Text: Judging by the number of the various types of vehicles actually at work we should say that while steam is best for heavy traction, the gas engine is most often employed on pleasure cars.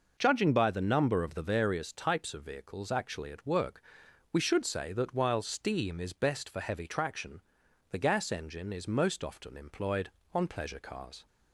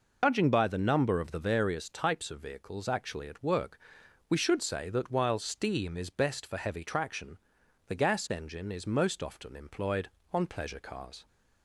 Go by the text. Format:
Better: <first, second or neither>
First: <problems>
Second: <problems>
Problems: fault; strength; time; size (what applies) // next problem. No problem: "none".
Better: first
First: pauses between "work" and "we"; noticeable; at 3.8 s; 0.52 s long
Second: loses the start of "Judging"; at 0.2 s; 80 ms // pauses between "work" and "we"; noticeable; at 3.7 s; 0.52 s long